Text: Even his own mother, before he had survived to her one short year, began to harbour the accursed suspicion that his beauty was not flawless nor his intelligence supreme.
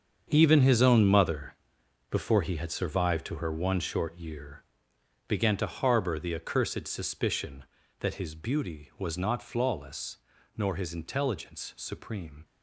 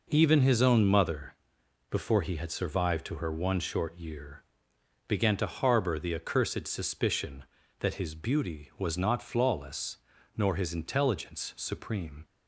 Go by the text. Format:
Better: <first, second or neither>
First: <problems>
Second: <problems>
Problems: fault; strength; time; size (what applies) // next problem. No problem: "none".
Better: second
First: gets quieter; strong; throughout; 12.5 dB // pauses between "flawless" and "nor"; slight; at 10.1 s; 0.36 s long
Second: pauses between "flawless" and "nor"; slight; at 9.9 s; 0.36 s long